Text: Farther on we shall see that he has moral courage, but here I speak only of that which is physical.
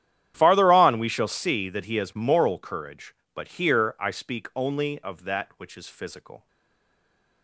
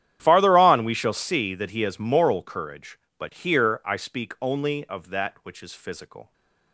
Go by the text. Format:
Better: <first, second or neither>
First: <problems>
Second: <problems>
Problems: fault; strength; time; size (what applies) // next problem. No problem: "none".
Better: second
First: starts louder than the rest; strong; until 1.3 s; 10.5 dB // stays silent after the last word; from 6.4 s on; 1.0 s long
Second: starts louder than the rest; strong; until 1.2 s; 10.5 dB